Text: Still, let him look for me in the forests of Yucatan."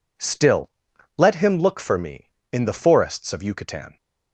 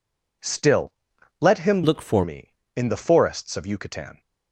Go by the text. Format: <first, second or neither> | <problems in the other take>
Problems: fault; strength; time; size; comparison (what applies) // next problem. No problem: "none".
first | changes voice from "look" to "for"; from 1.8 to 2.2 s; 0.4 s long